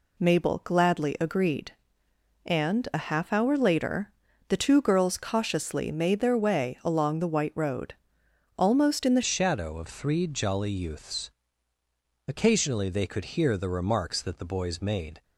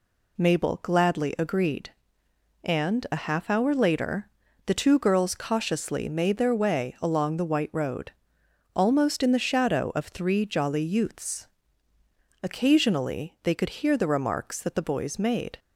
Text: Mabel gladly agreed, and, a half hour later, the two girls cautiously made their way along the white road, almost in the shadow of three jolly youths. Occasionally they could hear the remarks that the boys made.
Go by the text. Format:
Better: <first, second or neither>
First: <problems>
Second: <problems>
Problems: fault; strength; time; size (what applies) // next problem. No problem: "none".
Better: second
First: changes voice at "shadow"; from 9.2 s on; 6.0 s long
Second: none